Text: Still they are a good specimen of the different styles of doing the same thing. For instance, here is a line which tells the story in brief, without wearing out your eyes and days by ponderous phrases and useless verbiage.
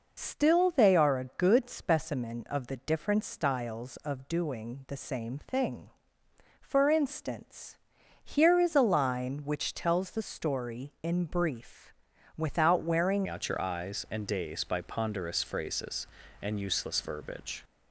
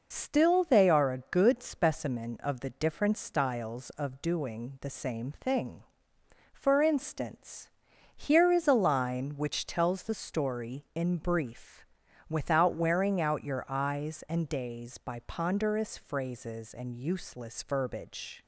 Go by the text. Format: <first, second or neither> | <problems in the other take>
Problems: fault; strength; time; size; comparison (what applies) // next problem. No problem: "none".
second | changes voice at "out"; from 13.2 s on; 4.4 s long